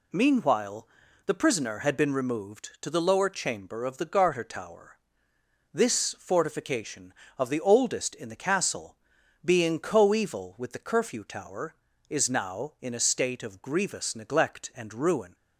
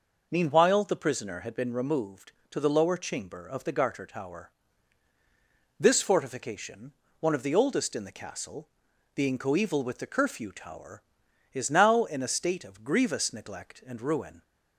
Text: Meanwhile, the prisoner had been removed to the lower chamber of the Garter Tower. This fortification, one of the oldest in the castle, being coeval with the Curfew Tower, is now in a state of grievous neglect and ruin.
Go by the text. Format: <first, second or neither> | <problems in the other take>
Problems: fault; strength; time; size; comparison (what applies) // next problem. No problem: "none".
second | skips "one"; at 7.2 s